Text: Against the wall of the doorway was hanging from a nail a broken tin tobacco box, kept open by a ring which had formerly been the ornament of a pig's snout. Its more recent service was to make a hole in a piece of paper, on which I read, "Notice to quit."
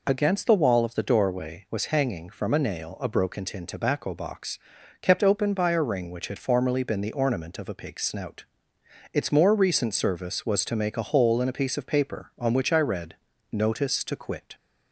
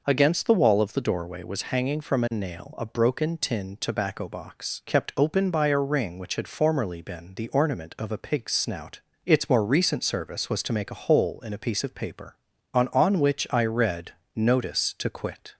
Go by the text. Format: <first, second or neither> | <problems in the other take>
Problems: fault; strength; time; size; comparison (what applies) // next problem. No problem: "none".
first | says "on" twice; at 12.9 s